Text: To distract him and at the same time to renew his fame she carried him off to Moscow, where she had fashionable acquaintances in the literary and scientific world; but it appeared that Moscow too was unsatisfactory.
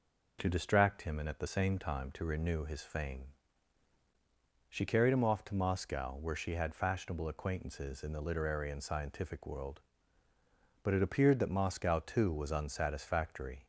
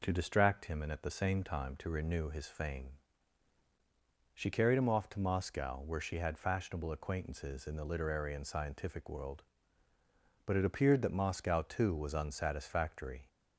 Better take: neither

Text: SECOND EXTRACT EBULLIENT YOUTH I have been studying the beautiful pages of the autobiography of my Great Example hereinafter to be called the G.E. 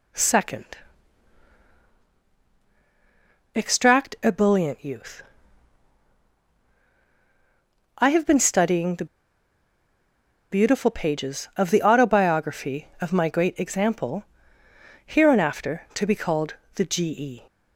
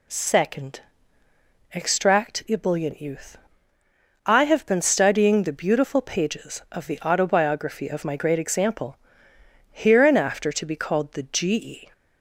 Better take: second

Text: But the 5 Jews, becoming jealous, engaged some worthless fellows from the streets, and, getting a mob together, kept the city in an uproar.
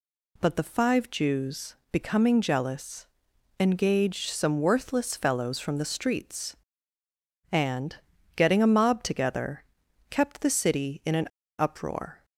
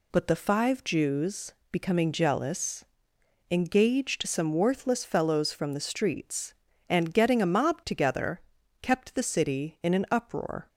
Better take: second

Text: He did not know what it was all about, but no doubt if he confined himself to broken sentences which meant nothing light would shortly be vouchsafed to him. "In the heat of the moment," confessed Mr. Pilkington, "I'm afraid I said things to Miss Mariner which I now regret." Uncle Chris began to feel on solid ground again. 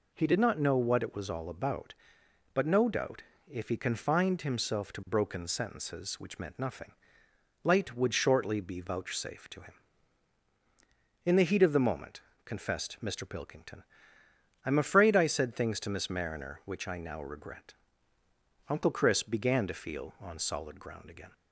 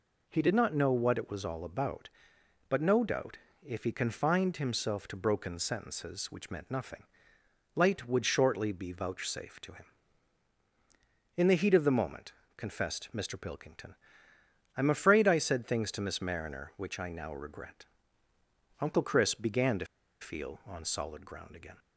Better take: first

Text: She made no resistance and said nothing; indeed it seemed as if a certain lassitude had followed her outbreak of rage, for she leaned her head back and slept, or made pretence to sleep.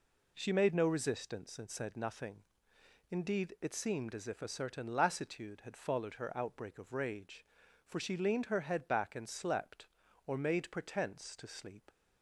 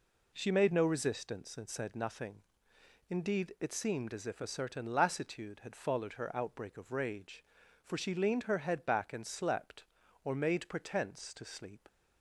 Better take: neither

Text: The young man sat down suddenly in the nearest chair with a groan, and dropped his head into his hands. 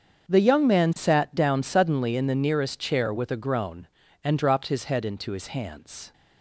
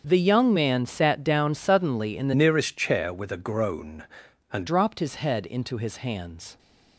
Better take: first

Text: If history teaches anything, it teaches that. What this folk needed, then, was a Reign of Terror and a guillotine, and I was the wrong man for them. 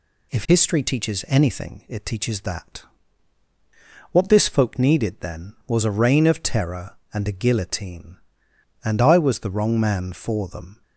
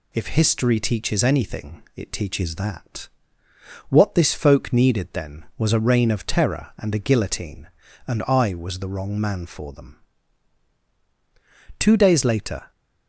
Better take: first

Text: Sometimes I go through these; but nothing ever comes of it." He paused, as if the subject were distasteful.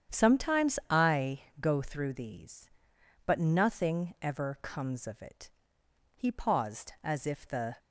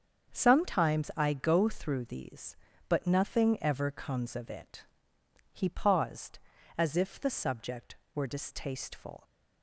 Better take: second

